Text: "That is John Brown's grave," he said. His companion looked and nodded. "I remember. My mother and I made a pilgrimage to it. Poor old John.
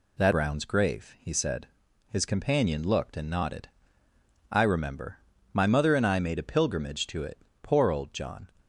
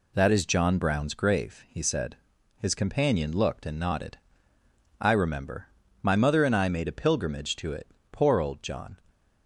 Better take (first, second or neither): second